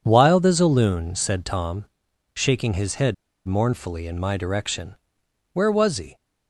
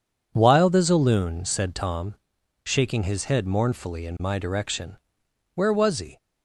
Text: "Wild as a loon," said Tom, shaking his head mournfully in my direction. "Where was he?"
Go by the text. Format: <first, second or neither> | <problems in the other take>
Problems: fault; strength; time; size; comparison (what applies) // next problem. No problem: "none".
second | pauses between "head" and "mournfully"; slight; at 3.1 s; 0.32 s long